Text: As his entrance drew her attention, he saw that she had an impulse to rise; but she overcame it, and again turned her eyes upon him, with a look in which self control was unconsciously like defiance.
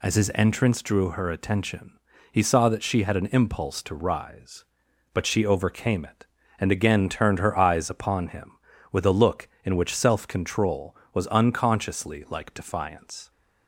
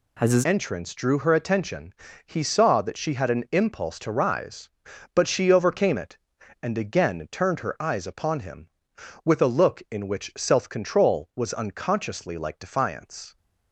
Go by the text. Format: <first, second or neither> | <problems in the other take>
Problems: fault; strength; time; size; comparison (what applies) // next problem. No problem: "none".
first | changes voice at "entrance"; from 0.4 s on; 12.9 s long